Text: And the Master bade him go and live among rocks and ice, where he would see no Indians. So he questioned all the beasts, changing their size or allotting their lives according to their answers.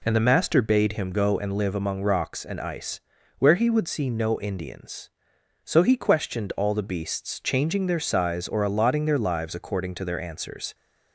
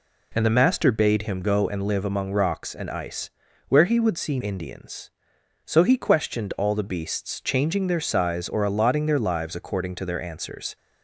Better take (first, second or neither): first